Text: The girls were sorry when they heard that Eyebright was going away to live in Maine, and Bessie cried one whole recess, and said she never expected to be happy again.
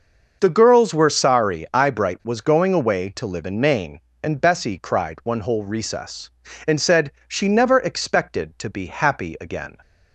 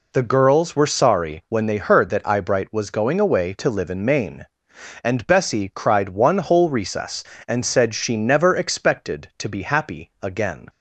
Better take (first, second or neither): second